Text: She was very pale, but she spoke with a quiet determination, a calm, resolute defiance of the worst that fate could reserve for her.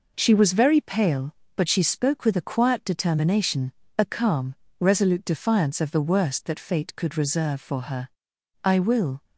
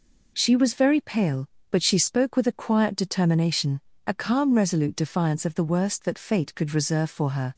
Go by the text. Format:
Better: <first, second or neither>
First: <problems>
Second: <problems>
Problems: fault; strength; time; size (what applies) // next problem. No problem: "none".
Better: second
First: goes on to say "I will"; from 8.6 s on; 0.60 s long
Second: none